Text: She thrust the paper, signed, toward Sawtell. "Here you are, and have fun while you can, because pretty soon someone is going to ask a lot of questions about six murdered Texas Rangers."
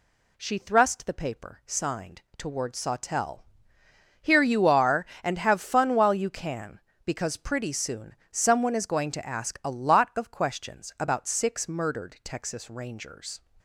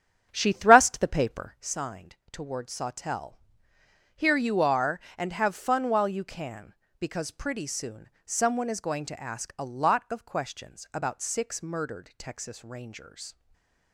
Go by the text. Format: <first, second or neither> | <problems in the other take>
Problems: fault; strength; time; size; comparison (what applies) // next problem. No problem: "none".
first | starts louder than the rest; strong; until 1.7 s; 8.5 dB // pauses between "soon" and "someone"; slight; at 8.0 s; 0.16 s long; slight in the first // stays silent after the last word; slight; from 13.3 s on; 0.6 s long